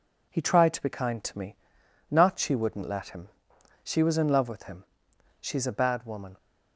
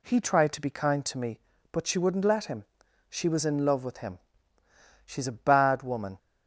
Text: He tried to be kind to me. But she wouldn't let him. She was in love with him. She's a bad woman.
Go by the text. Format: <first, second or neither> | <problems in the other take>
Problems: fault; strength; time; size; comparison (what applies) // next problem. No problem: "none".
second | says "Not" for "But"; at 2.1 s